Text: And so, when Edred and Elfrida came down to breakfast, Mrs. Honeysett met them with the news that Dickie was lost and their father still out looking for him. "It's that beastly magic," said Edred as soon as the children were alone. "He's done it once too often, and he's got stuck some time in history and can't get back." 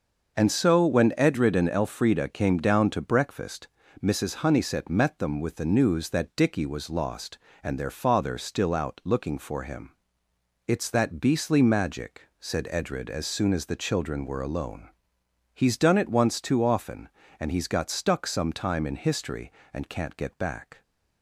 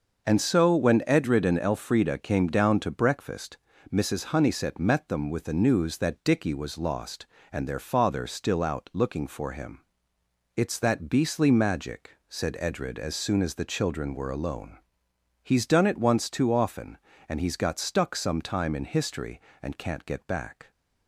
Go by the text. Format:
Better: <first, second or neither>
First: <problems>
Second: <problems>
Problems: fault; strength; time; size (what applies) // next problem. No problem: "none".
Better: neither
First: starts louder than the rest; noticeable; until 1.4 s; 6 dB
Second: starts louder than the rest; noticeable; until 1.3 s; 6 dB